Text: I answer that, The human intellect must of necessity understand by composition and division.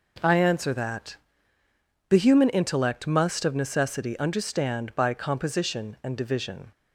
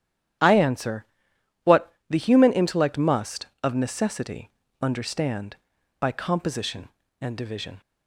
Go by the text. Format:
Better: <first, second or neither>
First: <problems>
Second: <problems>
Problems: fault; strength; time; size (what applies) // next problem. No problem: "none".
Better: first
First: none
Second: starts louder than the rest; strong; until 2.1 s; 10.5 dB // says "what" for "that"; at 1.6 s // pauses between "necessity" and "understand"; slight; at 4.5 s; 0.32 s long